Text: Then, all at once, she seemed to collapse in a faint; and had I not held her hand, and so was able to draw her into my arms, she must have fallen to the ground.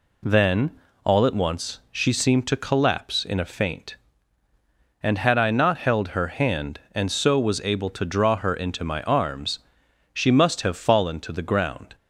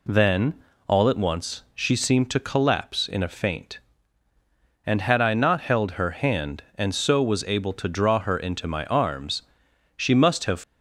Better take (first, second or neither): first